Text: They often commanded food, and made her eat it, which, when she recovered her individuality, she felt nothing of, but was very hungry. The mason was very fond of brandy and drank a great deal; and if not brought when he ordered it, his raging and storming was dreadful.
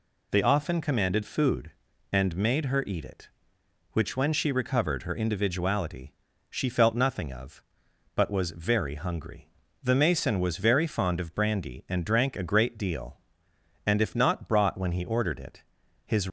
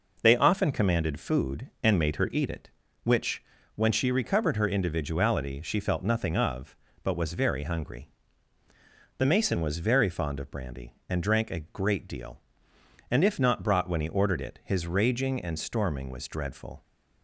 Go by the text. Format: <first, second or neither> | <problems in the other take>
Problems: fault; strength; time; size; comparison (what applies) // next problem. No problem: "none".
second | stops before "raging and storming was dreadful"; at 16.2 s